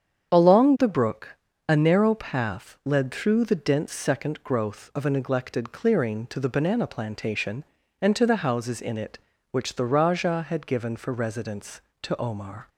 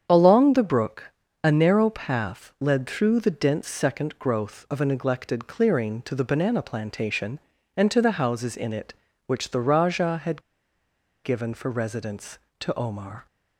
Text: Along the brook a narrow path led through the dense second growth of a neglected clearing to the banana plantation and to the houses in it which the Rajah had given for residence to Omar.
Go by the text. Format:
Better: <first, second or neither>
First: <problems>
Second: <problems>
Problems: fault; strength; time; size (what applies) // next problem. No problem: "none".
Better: first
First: starts louder than the rest; strong; until 1.3 s; 8 dB // pauses between "brook" and "a"; slight; at 1.3 s; 0.30 s long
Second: starts louder than the rest; strong; until 1.1 s; 8 dB // pauses between "brook" and "a"; slight; at 1.1 s; 0.30 s long // pauses between "had" and "given"; noticeable; at 10.4 s; 0.82 s long